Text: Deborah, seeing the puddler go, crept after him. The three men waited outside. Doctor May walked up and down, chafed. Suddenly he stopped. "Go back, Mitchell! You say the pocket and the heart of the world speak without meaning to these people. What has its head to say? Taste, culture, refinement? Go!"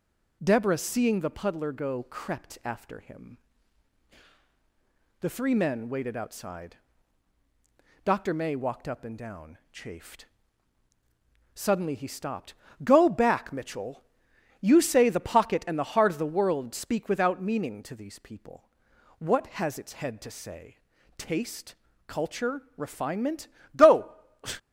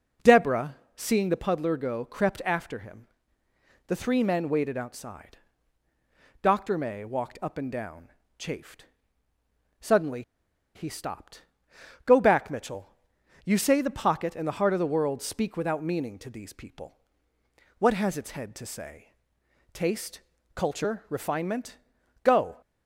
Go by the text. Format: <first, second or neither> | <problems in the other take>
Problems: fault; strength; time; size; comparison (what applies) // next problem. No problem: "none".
first | pauses between "Suddenly" and "he"; noticeable; at 10.2 s; 0.53 s long